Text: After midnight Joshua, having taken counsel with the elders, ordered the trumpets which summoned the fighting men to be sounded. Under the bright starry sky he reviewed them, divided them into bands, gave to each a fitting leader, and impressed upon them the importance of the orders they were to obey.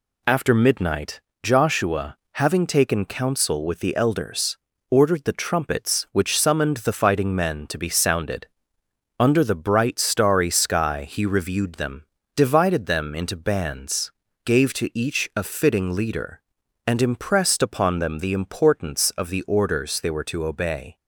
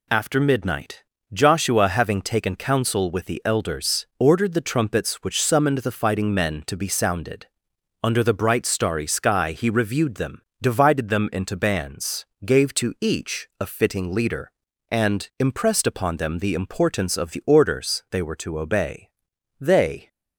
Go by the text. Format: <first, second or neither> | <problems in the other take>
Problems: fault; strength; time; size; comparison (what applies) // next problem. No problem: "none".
first | pauses between "midnight" and "Joshua"; slight; at 1.0 s; 0.32 s long; slight in the first // goes on to say "They"; slight; from 19.5 s on; 0.48 s long